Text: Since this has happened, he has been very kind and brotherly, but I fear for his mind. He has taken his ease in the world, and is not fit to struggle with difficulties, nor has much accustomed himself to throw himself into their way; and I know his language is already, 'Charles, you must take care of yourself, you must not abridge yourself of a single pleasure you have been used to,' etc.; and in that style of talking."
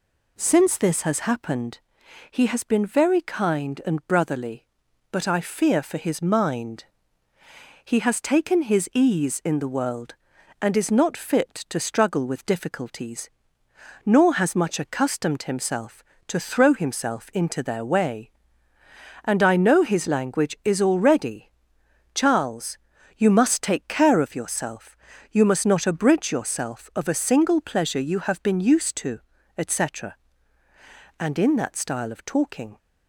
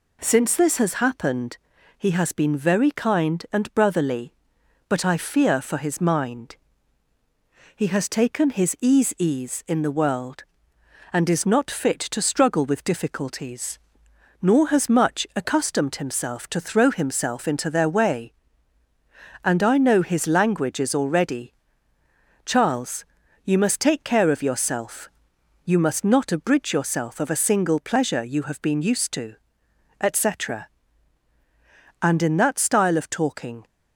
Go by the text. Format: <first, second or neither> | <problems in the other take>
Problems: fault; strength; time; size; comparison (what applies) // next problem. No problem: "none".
first | says "ease" twice; at 9.1 s